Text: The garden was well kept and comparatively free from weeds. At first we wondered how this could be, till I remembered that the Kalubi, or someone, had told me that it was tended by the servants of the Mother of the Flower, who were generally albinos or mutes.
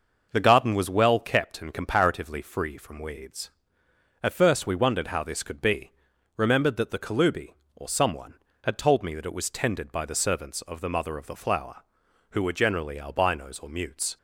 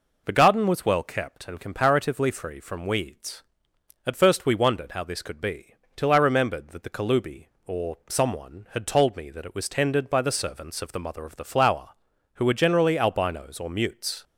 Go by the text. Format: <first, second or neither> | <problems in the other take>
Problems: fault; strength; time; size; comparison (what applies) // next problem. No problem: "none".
second | skips "till I"; at 6.1 s